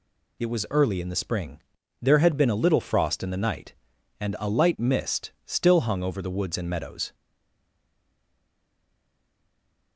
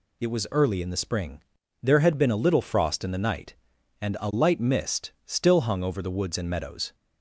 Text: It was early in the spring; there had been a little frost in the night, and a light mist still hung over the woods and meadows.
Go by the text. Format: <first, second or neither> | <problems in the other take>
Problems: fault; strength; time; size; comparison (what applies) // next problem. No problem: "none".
second | stays silent after the last word; strong; from 7.1 s on; 2.8 s long